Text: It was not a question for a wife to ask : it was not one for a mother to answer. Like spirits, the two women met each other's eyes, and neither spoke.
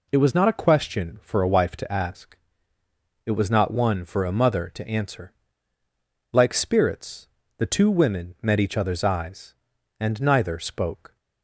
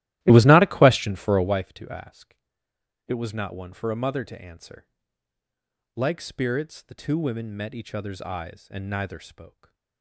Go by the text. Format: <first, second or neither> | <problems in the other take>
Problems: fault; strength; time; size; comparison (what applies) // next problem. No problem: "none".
first | starts louder than the rest; strong; until 1.7 s; 15.5 dB // stays silent after the last word; slight; from 9.4 s on; 0.6 s long